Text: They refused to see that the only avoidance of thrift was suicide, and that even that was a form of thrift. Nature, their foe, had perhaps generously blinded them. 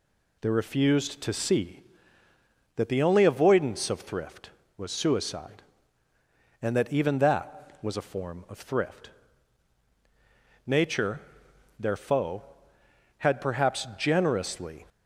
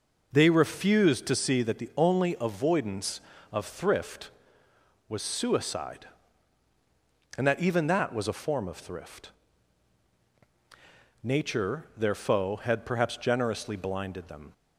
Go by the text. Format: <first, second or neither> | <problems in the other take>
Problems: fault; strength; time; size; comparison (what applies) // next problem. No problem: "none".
second | stops before "blinded them"; at 14.8 s